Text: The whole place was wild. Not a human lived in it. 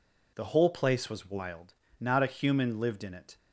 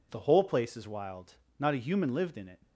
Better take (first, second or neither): first